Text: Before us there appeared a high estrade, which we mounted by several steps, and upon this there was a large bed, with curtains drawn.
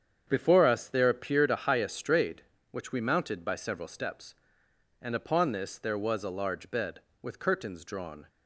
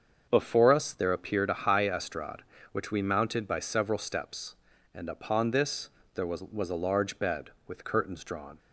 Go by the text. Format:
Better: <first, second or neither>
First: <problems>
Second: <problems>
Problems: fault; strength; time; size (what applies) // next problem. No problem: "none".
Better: first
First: starts louder than the rest; strong; until 1.2 s; 8 dB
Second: starts louder than the rest; until 1.3 s; 7 dB // pauses between "this" and "there"; slight; at 5.8 s; 0.28 s long // says "was" twice; at 6.4 s